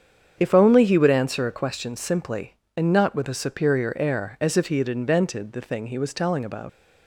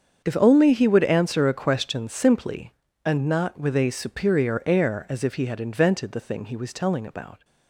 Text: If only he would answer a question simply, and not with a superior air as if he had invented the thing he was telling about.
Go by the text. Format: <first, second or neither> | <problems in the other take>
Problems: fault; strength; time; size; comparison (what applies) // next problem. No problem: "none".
second | starts louder than the rest; strong; until 1.3 s; 7.5 dB; strong in the second // leaves "about" unfinished; at 6.6 s; 95 ms